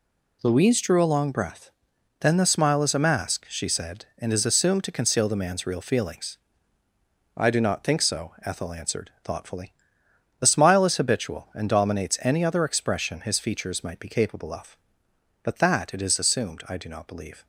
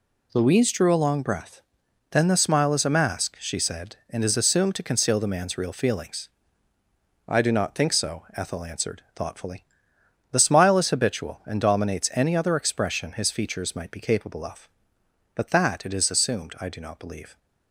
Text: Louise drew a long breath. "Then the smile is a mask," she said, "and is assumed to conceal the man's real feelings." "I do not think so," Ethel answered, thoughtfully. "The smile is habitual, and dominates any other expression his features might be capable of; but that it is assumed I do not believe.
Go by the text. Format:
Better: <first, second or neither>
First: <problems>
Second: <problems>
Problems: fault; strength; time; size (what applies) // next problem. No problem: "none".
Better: neither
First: none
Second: none